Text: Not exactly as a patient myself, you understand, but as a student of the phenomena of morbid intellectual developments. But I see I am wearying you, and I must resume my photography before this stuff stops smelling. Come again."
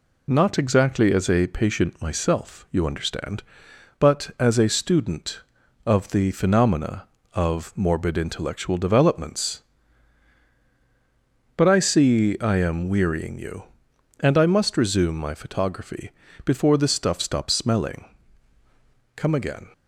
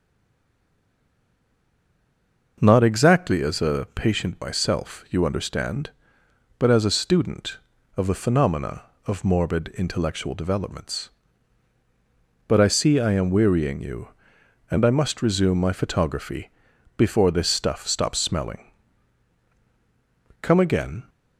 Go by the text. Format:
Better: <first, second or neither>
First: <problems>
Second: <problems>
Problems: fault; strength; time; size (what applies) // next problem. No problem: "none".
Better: first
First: pauses between "photography" and "before"; slight; at 16.1 s; 0.34 s long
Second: stays silent before the first word; strong; until 2.5 s; 2.5 s long // pauses between "photography" and "before"; noticeable; at 16.4 s; 0.48 s long